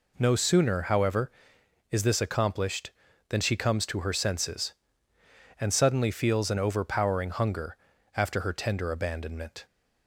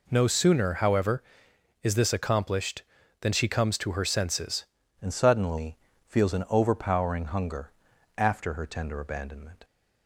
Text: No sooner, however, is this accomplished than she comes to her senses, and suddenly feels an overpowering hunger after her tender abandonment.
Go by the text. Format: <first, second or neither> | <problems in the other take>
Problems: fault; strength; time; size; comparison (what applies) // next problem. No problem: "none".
first | changes voice at "and"; from 5.0 s on; 4.6 s long // pauses between "suddenly" and "feels"; slight; at 5.7 s; 0.32 s long // pauses between "hunger" and "after"; at 7.7 s; 0.44 s long; also in the first